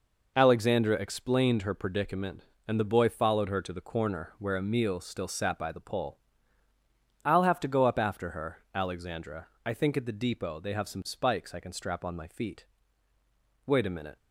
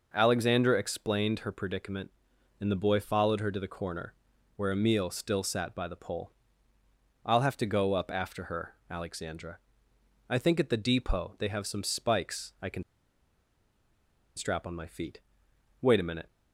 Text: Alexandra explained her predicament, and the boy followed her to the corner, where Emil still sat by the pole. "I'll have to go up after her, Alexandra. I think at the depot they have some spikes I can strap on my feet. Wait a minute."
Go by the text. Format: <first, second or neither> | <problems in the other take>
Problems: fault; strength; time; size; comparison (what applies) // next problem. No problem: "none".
first | pauses between "can" and "strap"; strong; at 12.8 s; 1.5 s long